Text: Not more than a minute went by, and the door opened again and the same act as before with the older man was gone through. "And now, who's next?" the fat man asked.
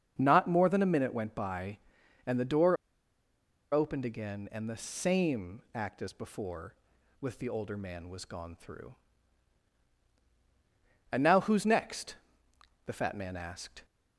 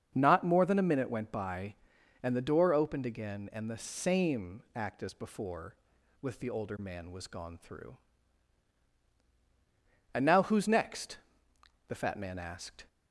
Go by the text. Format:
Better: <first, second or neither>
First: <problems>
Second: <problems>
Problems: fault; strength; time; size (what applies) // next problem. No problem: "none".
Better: second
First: starts louder than the rest; until 1.1 s; 7 dB // pauses between "door" and "opened"; noticeable; at 2.7 s; 0.96 s long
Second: starts louder than the rest; until 1.1 s; 7 dB